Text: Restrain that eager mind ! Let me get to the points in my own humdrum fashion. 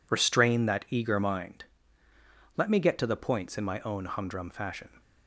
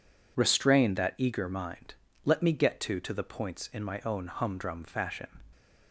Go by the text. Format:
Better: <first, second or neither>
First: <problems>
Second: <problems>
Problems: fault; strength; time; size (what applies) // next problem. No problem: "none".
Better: first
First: none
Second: says "to" twice; at 3.0 s